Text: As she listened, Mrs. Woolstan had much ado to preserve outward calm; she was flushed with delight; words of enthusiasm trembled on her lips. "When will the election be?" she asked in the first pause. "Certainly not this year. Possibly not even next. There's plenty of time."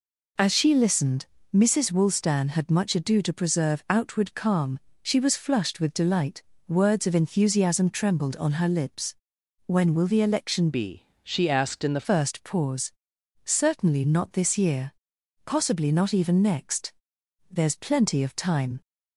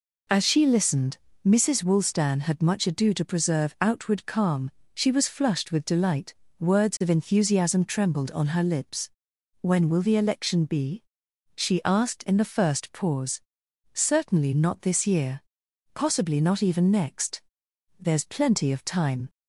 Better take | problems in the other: second | changes voice from "be" to "the"; from 10.7 to 12.0 s; 1.3 s long

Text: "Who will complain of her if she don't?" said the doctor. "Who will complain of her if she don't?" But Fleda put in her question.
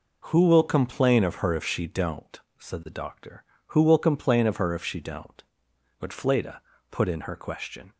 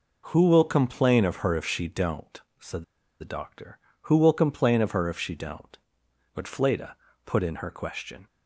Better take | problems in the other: first | pauses between "said" and "the"; at 2.8 s; 0.38 s long // pauses between "Fleda" and "put"; slight; at 6.9 s; 0.28 s long; slight in the first

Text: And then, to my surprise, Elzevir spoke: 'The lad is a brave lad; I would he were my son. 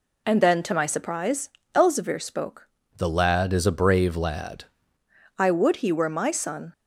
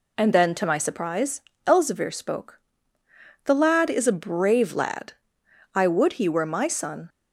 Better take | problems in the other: second | changes voice from "The" to "lad"; from 2.9 to 4.6 s; 1.7 s long

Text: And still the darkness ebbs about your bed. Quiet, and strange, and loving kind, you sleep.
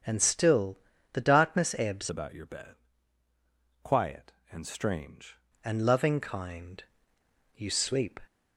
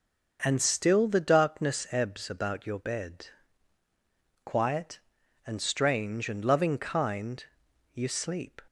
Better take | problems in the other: second | starts louder than the rest; strong; until 1.4 s; 7.5 dB; noticeable in the second // pauses between "still" and "the"; slight; at 0.7 s; 0.36 s long // changes voice from "about" to "strange"; from 2.0 to 5.3 s; 3.3 s long

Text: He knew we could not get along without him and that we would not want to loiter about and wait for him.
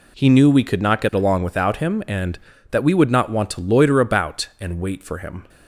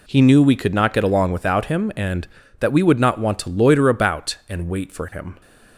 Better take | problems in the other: neither | none

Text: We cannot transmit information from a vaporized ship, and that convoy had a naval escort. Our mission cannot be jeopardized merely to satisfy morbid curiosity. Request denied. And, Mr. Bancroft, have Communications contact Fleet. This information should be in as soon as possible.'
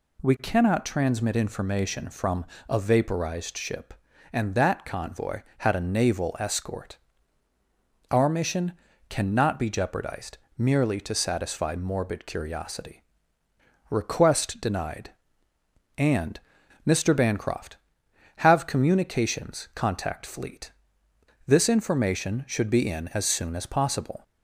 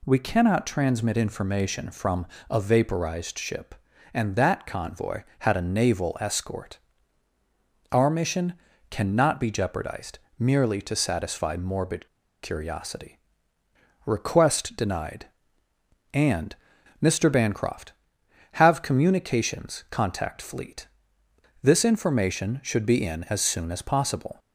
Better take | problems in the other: first | pauses between "from" and "a"; slight; at 2.2 s; 0.24 s long; slight in the first // pauses between "mission" and "cannot"; slight; at 8.5 s; 0.36 s long; slight in the first // pauses between "jeopardized" and "merely"; slight; at 10.1 s; 0.20 s long; slight in the first // pauses between "morbid" and "curiosity"; at 12.0 s; 0.37 s long

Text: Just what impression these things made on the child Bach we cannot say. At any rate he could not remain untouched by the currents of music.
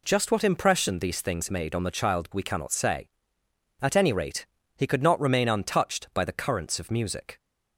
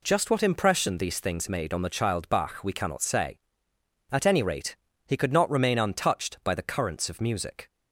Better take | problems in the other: second | skips "Bach"; at 2.3 s // pauses between "rate" and "he"; slight; at 4.4 s; 0.32 s long; slight in the second

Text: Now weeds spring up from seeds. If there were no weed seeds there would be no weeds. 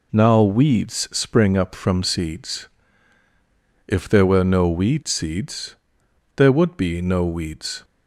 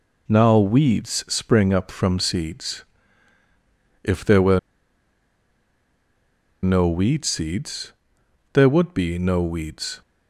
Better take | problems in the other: first | pauses between "were" and "no"; strong; at 4.5 s; 2.0 s long // pauses between "seeds" and "there"; noticeable; at 7.9 s; 0.62 s long; noticeable in the first

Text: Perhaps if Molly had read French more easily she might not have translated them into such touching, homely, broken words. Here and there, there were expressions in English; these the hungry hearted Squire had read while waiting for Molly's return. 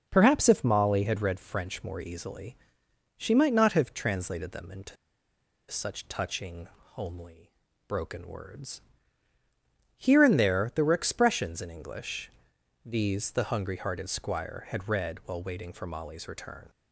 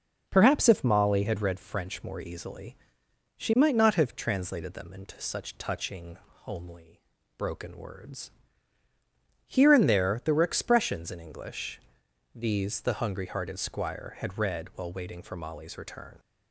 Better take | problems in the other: second | pauses between "easily" and "she"; noticeable; at 2.5 s; 0.64 s long; noticeable in the second // pauses between "into" and "such"; noticeable; at 4.9 s; 0.74 s long

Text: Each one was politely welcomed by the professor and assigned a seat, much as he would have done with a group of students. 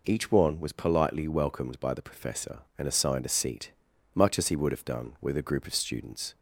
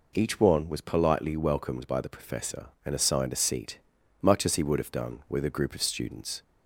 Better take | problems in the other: neither | none

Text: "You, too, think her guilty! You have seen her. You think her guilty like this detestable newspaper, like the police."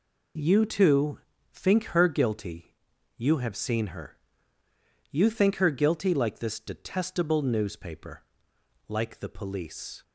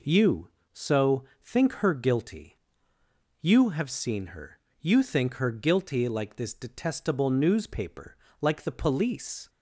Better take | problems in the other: first | says "so" for "too"; at 0.7 s

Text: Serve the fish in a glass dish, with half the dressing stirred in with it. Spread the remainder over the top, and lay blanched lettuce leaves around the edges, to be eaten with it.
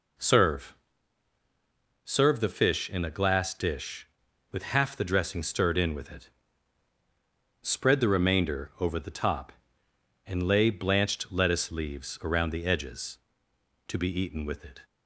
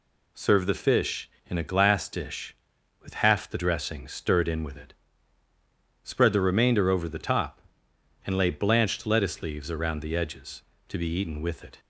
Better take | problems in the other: second | says "Serve" twice; at 2.0 s

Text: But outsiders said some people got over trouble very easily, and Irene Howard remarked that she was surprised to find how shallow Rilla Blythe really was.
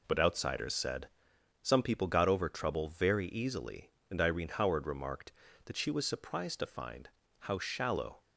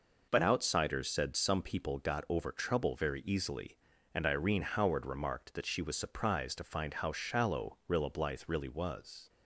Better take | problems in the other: second | pauses between "said" and "some"; noticeable; at 1.0 s; 0.54 s long // pauses between "find" and "how"; slight; at 7.0 s; 0.30 s long // stops before "Rilla Blythe really was"; at 8.2 s

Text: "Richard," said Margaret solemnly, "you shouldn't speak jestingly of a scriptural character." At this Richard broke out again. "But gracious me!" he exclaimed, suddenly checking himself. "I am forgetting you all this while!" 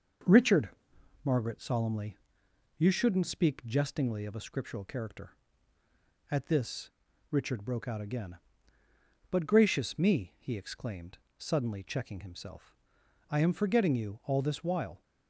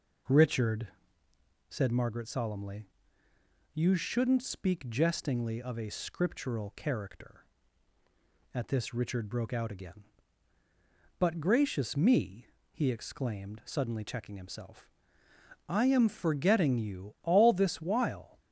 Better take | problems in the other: second | skips "said"; at 0.9 s // pauses between "this" and "Richard"; at 6.9 s; 0.40 s long

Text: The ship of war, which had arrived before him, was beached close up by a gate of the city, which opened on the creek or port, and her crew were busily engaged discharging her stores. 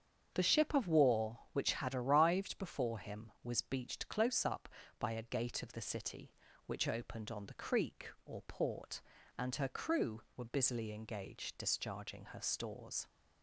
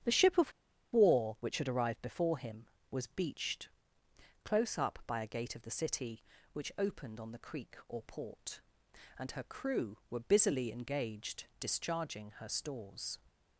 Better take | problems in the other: first | starts louder than the rest; strong; until 1.4 s; 8.5 dB; strong in the first // pauses between "of" and "war"; at 0.5 s; 0.41 s long // pauses between "beached" and "close"; noticeable; at 3.6 s; 0.74 s long // pauses between "engaged" and "discharging"; slight; at 11.4 s; 0.16 s long

